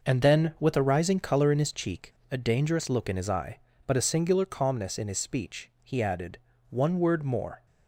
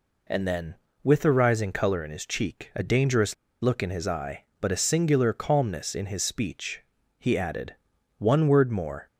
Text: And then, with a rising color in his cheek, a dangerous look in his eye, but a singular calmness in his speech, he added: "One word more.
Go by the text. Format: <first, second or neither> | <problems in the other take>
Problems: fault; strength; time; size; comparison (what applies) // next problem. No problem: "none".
first | pauses between "dangerous" and "look"; slight; at 3.3 s; 0.26 s long